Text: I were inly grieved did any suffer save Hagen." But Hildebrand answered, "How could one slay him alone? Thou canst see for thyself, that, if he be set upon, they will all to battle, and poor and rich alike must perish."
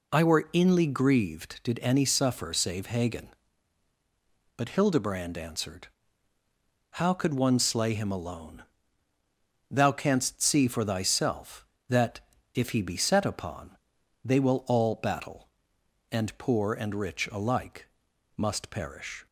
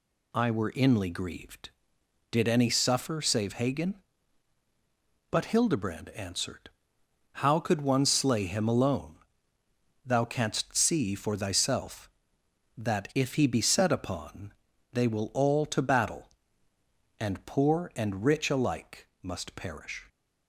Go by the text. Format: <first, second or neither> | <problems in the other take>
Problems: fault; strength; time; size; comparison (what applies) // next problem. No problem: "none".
second | skips "to"; at 14.9 s // pauses between "alike" and "must"; noticeable; at 17.8 s; 0.48 s long; slight in the second